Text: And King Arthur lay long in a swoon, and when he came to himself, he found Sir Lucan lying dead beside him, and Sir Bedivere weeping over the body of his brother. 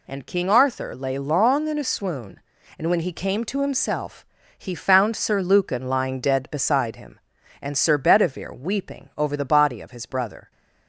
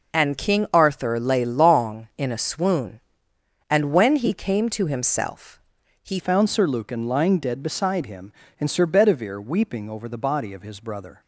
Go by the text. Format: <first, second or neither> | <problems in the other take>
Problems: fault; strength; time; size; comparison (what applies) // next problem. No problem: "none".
first | changes voice at "found"; from 6.1 s on; 5.1 s long